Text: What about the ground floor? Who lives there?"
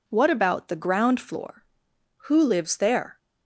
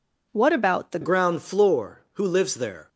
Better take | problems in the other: first | changes voice at "ground"; from 1.0 s on; 1.8 s long

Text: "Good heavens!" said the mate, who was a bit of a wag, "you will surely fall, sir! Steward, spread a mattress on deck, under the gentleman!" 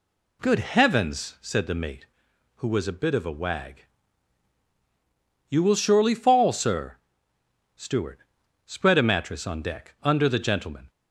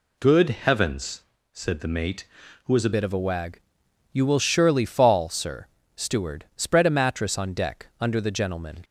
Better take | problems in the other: first | changes voice at "bit"; from 2.9 s on; 5.9 s long

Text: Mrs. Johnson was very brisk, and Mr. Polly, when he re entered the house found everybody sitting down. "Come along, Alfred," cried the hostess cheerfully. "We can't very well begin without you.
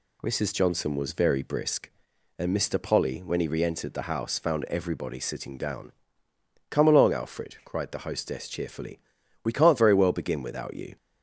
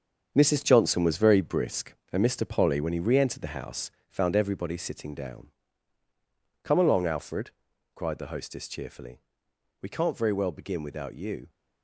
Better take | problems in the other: first | gets quieter; strong; throughout; 8.5 dB // pauses between "house" and "found"; slight; at 3.9 s; 0.16 s long

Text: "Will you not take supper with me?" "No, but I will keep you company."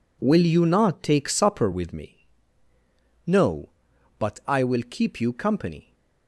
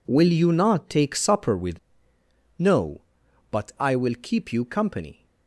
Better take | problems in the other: first | skips "me"; at 2.1 s

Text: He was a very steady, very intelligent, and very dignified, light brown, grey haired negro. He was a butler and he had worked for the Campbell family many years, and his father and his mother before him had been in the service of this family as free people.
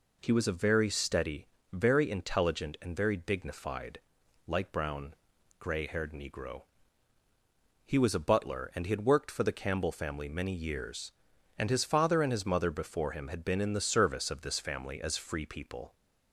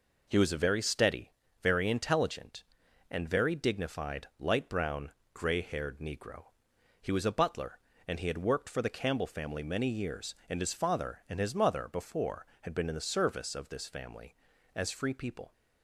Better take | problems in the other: first | skips "him"; at 12.5 s

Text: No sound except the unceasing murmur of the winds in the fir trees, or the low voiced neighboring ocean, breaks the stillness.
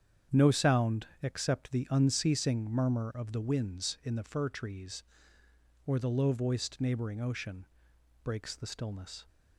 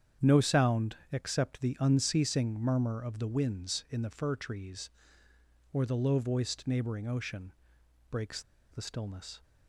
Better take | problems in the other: first | starts louder than the rest; strong; until 1.3 s; 8.5 dB; strong in the first // pauses between "sound" and "except"; slight; at 0.9 s; 0.16 s long; slight in the first // pauses between "breaks" and "the"; slight; at 8.4 s; 0.30 s long

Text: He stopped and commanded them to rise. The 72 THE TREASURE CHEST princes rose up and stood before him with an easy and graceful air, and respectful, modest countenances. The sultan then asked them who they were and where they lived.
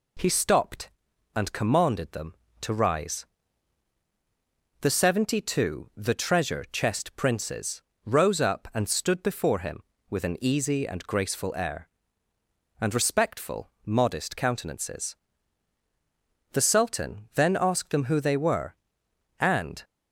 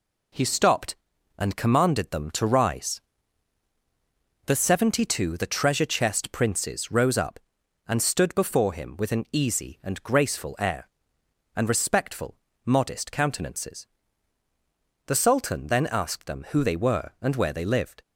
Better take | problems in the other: second | pauses between "princes" and "rose"; slight; at 7.8 s; 0.22 s long // stops before "where they lived"; at 19.8 s

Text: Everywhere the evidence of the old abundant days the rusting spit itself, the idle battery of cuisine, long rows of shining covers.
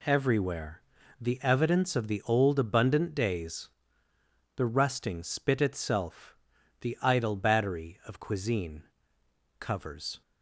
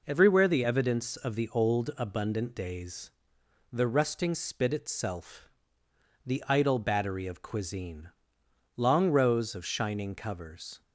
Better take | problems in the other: second | pauses between "Everywhere" and "the"; at 0.8 s; 0.38 s long // pauses between "days" and "the"; noticeable; at 3.6 s; 0.88 s long; noticeable in the second // skips "long rows of shining"; at 9.2 s

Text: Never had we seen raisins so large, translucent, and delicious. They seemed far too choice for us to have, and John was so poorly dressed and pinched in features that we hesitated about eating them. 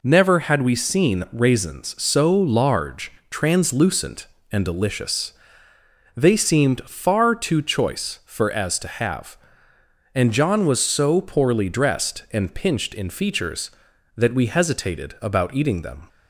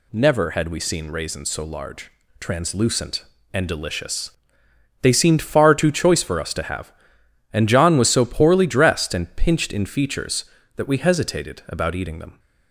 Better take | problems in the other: second | says "as" for "us"; at 8.5 s

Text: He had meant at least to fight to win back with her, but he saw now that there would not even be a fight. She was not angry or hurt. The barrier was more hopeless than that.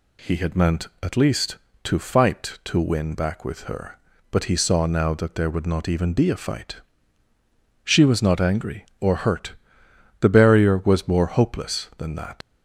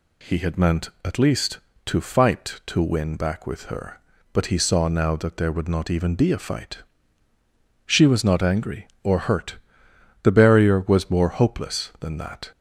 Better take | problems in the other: second | leaves "that" unfinished; at 12.4 s; 80 ms

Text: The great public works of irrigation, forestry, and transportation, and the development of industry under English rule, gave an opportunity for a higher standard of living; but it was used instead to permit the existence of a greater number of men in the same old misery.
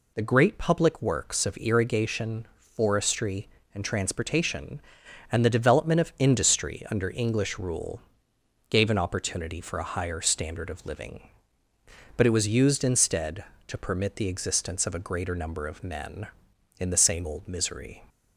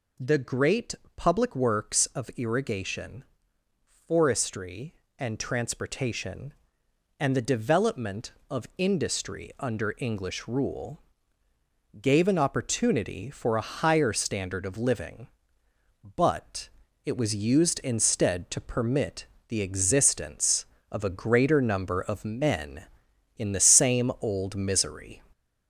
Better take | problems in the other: first | gets louder; noticeable; throughout; 4 dB // pauses between "great" and "public"; slight; at 0.9 s; 0.20 s long // pauses between "but" and "it"; slight; at 16.6 s; 0.36 s long // pauses between "permit" and "the"; slight; at 19.2 s; 0.22 s long

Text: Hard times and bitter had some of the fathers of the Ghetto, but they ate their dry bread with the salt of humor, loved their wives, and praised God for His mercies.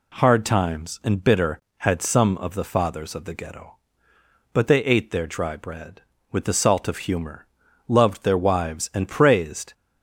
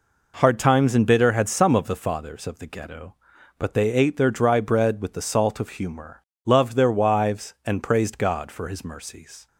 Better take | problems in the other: second | stops before "God for His mercies"; at 9.7 s

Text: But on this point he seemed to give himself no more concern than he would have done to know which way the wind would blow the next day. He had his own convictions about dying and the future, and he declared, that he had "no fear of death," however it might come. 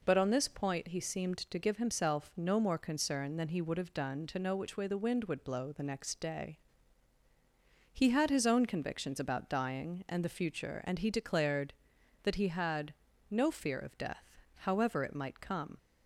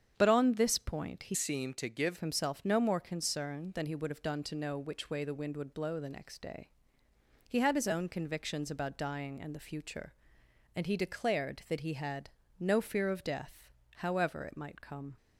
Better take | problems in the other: first | starts louder than the rest; strong; until 1.1 s; 8 dB // changes voice from "seemed" to "give"; from 1.3 to 2.1 s; 0.8 s long // pauses between "had" and "no"; slight; at 12.2 s; 0.32 s long; slight in the first

